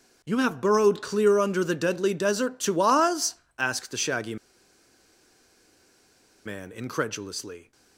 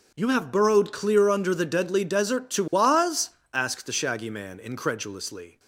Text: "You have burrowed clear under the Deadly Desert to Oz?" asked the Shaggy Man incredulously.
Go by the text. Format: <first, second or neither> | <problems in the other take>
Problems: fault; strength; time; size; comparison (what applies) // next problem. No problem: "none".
second | pauses between "Shaggy" and "Man"; strong; at 4.3 s; 2.0 s long